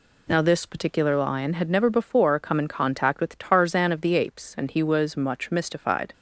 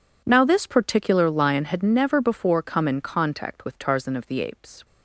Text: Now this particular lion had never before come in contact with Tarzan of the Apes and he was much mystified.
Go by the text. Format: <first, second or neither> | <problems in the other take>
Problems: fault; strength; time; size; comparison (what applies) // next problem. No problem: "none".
first | stops before "and he was much mystified"; at 4.8 s